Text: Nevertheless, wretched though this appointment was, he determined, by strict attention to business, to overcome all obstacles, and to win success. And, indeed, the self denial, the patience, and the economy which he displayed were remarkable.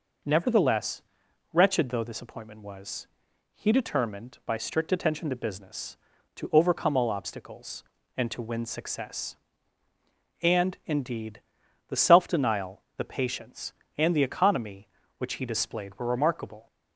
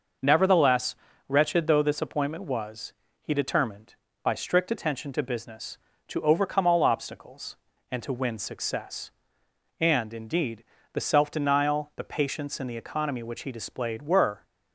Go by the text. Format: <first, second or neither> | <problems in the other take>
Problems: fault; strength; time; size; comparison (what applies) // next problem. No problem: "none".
first | stops before "remarkable"; at 14.4 s